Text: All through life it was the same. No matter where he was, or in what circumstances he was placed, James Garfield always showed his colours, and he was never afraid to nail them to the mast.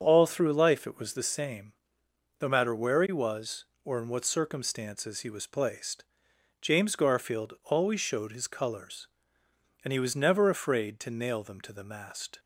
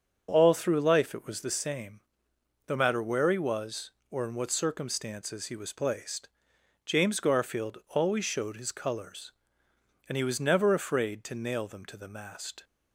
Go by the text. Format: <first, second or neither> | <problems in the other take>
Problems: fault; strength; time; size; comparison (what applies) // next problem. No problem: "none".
neither | starts louder than the rest; the same in both